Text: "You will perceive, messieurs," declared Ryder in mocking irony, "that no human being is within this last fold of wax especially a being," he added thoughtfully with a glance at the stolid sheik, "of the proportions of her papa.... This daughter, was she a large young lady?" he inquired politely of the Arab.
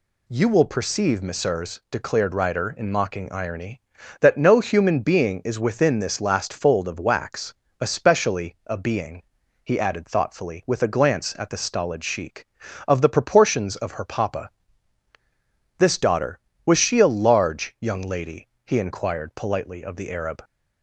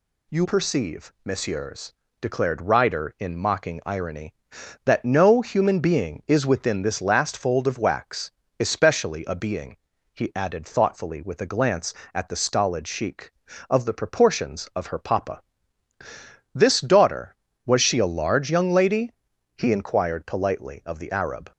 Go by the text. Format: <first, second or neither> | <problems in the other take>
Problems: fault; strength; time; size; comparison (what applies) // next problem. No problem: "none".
first | skips "will"; at 0.4 s // pauses between "wax" and "especially"; slight; at 8.3 s; 0.26 s long; slight in the first